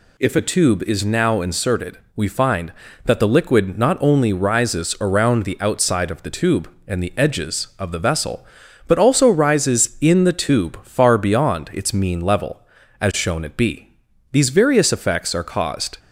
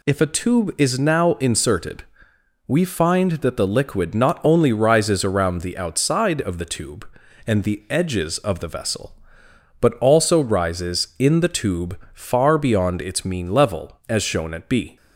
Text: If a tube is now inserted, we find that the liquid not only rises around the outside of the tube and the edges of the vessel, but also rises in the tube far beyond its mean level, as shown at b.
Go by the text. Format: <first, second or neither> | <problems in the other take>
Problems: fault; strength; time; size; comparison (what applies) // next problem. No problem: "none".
second | goes on to say "These various effects are caused"; strong; from 14.3 s on; 1.6 s long